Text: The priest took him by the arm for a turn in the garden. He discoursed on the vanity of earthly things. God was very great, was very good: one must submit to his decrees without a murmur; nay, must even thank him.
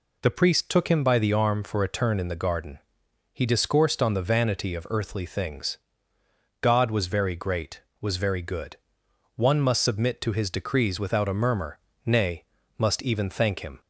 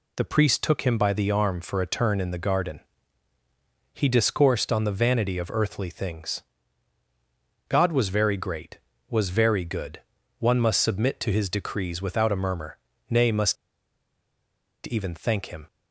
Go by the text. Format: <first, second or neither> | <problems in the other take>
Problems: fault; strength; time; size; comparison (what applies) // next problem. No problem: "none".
first | pauses between "must" and "even"; strong; at 13.5 s; 1.3 s long